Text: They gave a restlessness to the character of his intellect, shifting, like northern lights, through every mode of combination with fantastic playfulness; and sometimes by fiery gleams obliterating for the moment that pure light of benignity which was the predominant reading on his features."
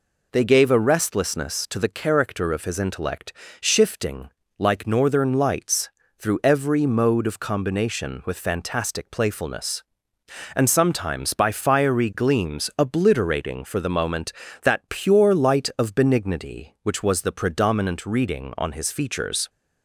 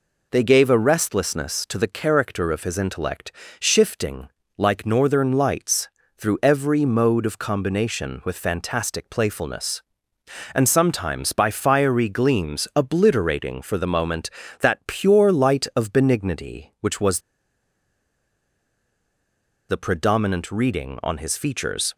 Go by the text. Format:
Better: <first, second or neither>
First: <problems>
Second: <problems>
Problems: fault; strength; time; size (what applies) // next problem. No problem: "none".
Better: first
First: none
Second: pauses between "was" and "the"; strong; at 17.2 s; 2.4 s long